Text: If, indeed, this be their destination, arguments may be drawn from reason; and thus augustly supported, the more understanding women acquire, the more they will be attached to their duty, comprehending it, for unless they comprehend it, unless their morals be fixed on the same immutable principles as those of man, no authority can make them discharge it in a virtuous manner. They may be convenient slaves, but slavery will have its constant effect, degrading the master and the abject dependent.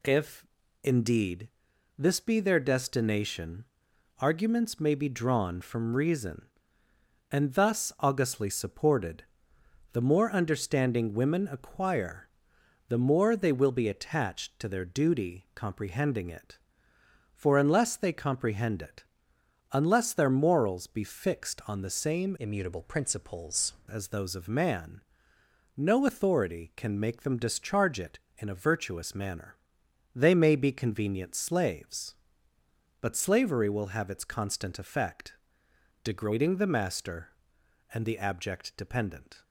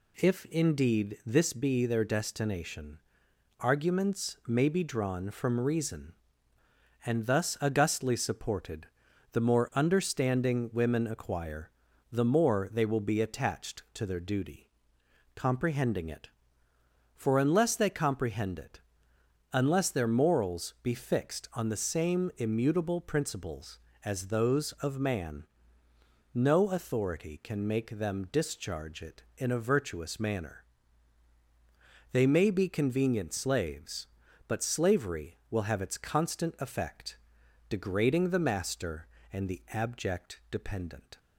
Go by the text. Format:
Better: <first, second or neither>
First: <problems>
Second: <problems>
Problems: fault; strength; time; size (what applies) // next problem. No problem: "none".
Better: second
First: changes voice from "immutable" to "principles"; from 22.3 to 23.7 s; 1.4 s long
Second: none